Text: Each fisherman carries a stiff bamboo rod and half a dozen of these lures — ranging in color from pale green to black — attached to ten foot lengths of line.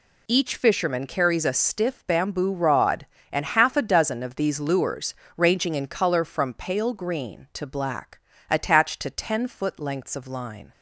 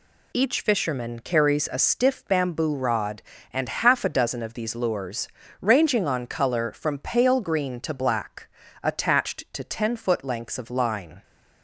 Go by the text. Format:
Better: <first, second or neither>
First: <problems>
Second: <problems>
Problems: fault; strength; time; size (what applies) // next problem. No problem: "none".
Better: first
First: none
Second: says "on" for "in"; at 6.0 s